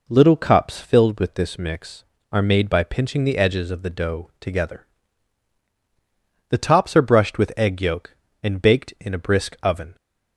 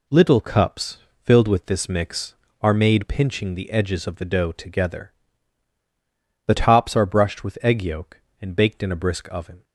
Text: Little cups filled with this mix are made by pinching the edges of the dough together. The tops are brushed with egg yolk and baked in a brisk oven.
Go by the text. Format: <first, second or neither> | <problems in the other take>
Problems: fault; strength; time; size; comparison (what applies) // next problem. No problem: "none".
first | pauses between "cups" and "filled"; slight; at 0.9 s; 0.26 s long // skips "by"; at 3.0 s